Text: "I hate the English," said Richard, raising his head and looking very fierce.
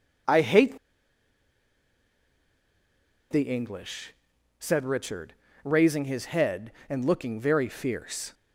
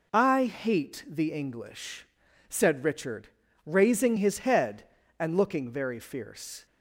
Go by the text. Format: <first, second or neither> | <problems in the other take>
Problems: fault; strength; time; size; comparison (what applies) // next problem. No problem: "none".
second | pauses between "hate" and "the"; strong; at 0.7 s; 2.5 s long